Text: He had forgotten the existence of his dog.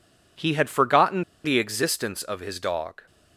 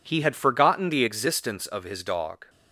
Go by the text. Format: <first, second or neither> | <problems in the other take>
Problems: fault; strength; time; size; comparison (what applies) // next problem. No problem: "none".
second | pauses between "forgotten" and "the"; slight; at 1.2 s; 0.21 s long